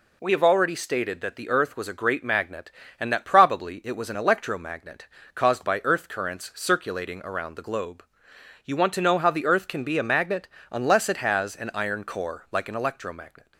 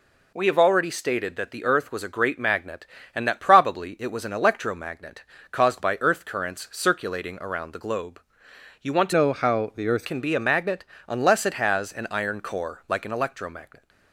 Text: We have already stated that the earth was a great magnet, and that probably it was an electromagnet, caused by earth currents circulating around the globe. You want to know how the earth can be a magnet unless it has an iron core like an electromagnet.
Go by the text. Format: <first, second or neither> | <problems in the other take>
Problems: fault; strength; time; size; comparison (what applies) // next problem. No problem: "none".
first | changes voice from "know" to "earth"; from 9.1 to 10.0 s; 0.9 s long // pauses between "magnet" and "unless"; slight; at 10.8 s; 0.22 s long; slight in the first